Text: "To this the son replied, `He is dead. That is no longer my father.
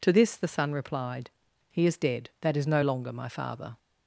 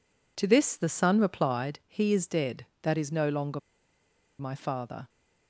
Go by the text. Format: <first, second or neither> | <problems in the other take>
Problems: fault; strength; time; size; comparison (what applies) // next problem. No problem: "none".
first | pauses between "longer" and "my"; noticeable; at 3.5 s; 0.80 s long